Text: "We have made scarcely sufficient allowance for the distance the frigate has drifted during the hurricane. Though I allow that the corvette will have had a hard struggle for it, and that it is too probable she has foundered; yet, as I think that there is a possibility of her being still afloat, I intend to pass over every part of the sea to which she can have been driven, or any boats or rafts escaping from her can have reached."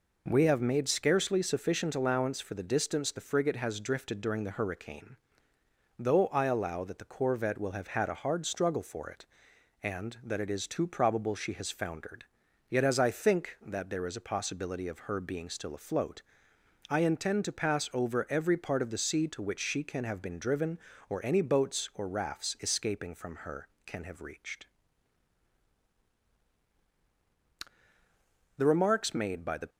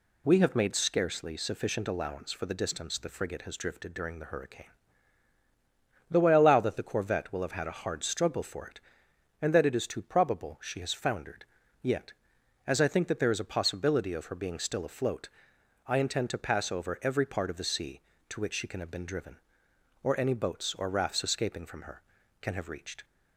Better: second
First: goes on to say "The remarks made by the"; noticeable; from 28.5 s on; 1.1 s long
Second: none

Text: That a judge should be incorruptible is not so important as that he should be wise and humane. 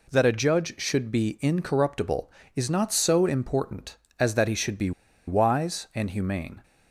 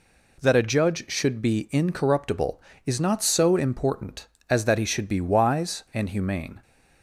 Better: second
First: pauses between "be" and "wise"; at 4.9 s; 0.36 s long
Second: none

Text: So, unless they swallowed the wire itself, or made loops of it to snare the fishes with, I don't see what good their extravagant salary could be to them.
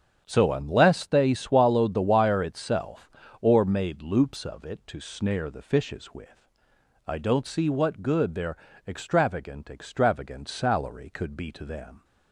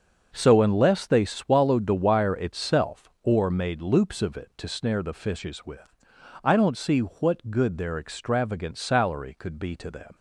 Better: second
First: starts louder than the rest; strong; until 1.2 s; 8 dB // pauses between "their" and "extravagant"; slight; at 8.5 s; 0.30 s long // says "extravagant" twice; at 9.6 s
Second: starts louder than the rest; until 1.3 s; 6 dB

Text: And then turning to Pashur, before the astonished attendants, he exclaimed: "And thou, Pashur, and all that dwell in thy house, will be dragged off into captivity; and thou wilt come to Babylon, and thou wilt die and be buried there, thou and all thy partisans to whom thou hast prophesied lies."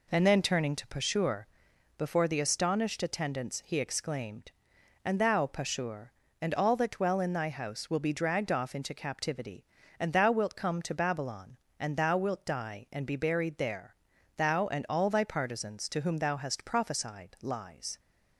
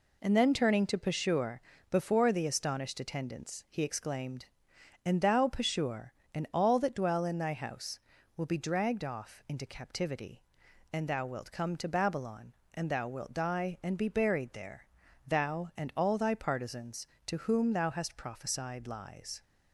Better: neither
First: none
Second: none

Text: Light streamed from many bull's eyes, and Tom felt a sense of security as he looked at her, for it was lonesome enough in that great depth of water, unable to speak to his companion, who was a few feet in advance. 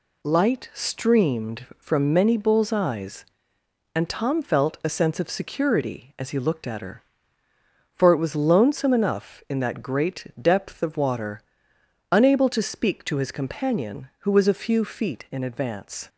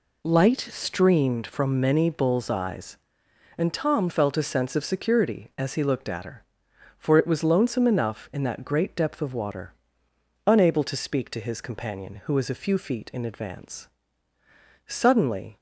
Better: first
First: none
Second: goes on to say "Suddenly"; noticeable; from 14.8 s on; 0.70 s long

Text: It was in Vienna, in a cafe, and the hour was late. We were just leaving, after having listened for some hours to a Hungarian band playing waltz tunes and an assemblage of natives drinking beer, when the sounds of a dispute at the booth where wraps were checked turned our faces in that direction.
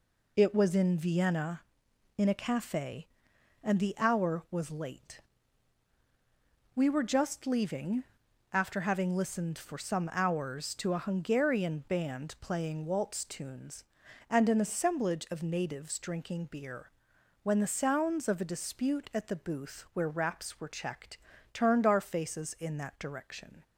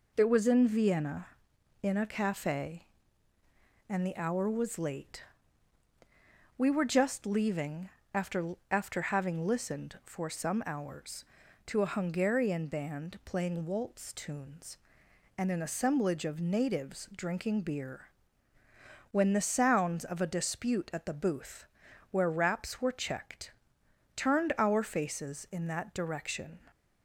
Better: first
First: pauses between "checked" and "turned"; slight; at 21.1 s; 0.34 s long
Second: says "after" twice; at 8.6 s // pauses between "booth" and "where"; noticeable; at 21.6 s; 0.46 s long // pauses between "checked" and "turned"; noticeable; at 23.4 s; 0.66 s long

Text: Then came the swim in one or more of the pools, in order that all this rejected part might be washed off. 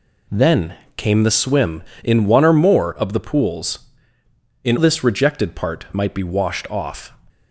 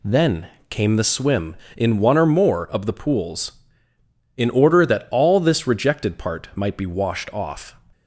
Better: second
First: pauses between "Then" and "came"; slight; at 0.7 s; 0.22 s long // skips "order that all"; at 4.7 s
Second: pauses between "Then" and "came"; slight; at 0.4 s; 0.22 s long

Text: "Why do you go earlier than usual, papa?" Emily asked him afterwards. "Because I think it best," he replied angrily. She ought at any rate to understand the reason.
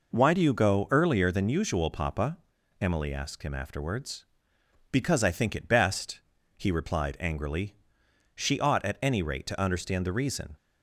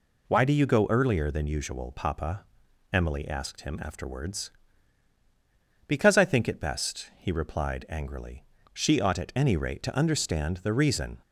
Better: neither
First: none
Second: none

